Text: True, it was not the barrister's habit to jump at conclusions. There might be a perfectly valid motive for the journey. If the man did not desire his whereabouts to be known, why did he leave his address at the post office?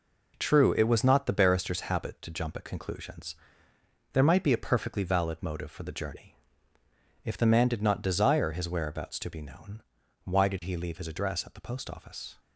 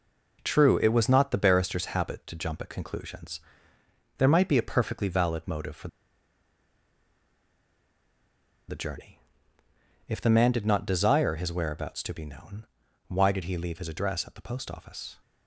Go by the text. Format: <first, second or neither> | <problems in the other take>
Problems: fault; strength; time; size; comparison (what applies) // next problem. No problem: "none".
first | pauses between "for" and "the"; strong; at 5.8 s; 2.8 s long